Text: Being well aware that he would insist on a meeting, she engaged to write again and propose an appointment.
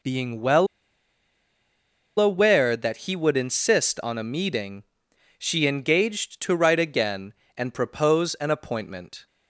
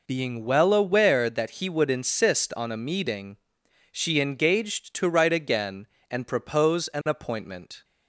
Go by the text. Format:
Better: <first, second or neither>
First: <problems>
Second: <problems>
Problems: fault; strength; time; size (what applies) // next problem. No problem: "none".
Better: second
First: pauses between "well" and "aware"; strong; at 0.6 s; 1.5 s long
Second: none